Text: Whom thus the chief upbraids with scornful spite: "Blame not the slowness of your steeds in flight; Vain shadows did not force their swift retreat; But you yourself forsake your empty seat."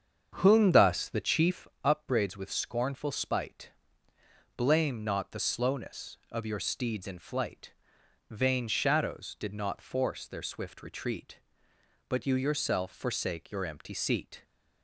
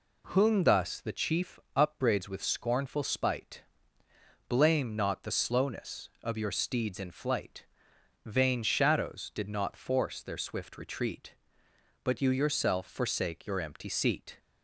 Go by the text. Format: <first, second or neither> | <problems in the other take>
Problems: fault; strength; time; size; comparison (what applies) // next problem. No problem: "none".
second | starts louder than the rest; strong; until 1.8 s; 7 dB // pauses between "chief" and "upbraids"; slight; at 1.6 s; 0.18 s long; slight in the second